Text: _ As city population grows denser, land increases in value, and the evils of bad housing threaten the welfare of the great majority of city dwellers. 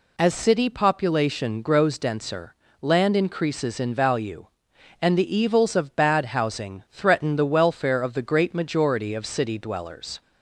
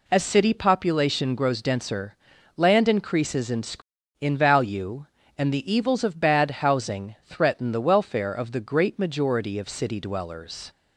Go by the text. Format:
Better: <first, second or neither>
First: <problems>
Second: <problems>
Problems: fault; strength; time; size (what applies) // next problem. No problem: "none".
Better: first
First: none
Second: says "in" twice; at 4.1 s